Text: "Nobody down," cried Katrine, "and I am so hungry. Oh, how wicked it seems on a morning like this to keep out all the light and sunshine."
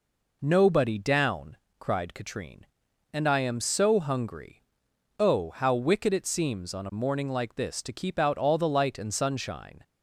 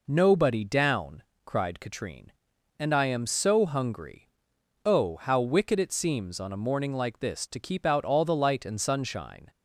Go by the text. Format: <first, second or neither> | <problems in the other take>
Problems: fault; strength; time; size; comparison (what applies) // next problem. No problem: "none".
neither | none